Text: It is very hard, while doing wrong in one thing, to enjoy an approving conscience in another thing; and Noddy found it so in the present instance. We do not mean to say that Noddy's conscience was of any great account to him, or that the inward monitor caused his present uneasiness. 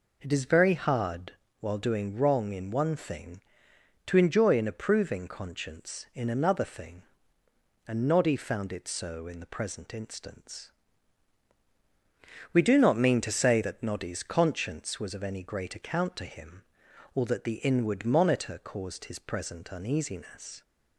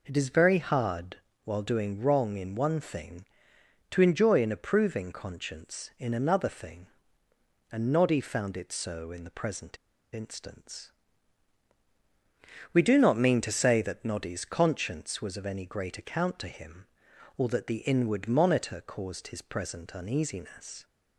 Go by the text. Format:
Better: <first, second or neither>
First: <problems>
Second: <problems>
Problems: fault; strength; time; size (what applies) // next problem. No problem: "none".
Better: first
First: none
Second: pauses between "present" and "instance"; at 9.7 s; 0.36 s long